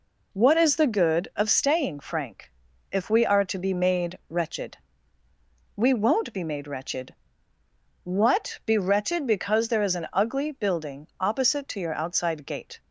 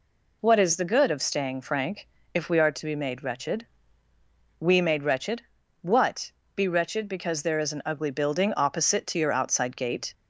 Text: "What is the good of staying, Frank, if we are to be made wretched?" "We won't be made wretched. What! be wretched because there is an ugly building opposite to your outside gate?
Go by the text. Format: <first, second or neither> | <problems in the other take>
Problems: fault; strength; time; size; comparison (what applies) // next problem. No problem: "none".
first | skips "won't be"; at 4.7 s